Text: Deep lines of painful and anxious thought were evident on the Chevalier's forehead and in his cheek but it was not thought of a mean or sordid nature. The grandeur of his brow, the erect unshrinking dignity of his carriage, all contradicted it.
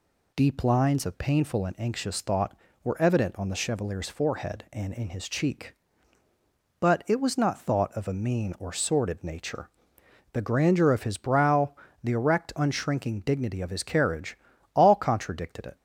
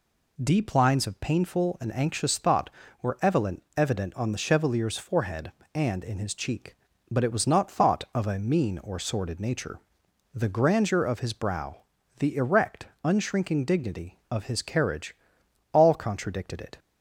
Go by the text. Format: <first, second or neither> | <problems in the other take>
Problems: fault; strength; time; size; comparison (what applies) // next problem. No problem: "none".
first | says "evident" twice; at 3.7 s // pauses between "erect" and "unshrinking"; slight; at 12.8 s; 0.18 s long